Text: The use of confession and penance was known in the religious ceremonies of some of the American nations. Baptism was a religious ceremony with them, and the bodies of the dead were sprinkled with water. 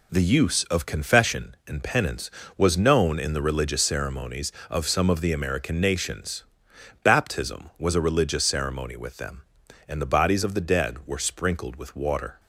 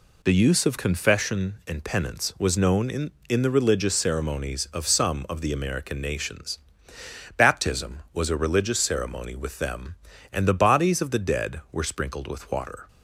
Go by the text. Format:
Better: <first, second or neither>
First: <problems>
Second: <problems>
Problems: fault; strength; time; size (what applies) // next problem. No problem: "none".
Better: first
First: none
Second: says "in" twice; at 3.2 s